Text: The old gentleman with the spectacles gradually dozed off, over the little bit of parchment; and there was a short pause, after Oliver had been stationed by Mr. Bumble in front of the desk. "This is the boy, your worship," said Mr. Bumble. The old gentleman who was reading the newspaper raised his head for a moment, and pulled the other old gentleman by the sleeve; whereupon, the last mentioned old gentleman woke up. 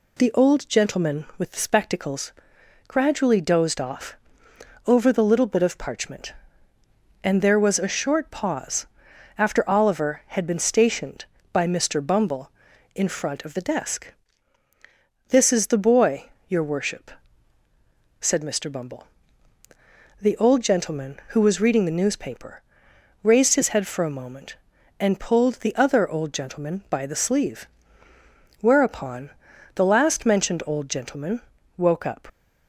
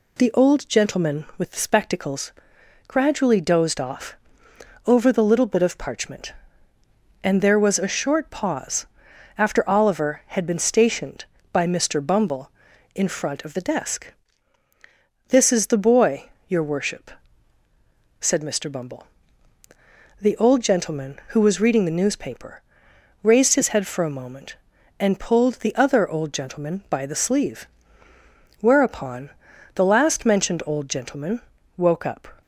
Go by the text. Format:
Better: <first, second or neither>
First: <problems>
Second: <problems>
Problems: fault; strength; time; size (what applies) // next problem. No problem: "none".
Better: second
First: pauses between "spectacles" and "gradually"; noticeable; at 2.3 s; 0.56 s long // pauses between "newspaper" and "raised"; noticeable; at 22.6 s; 0.60 s long // pauses between "gentleman" and "woke"; at 31.3 s; 0.38 s long // leaves "up" unfinished; at 32.2 s; 115 ms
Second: pauses between "spectacles" and "gradually"; noticeable; at 2.3 s; 0.56 s long // pauses between "newspaper" and "raised"; noticeable; at 22.6 s; 0.60 s long // pauses between "gentleman" and "woke"; at 31.3 s; 0.38 s long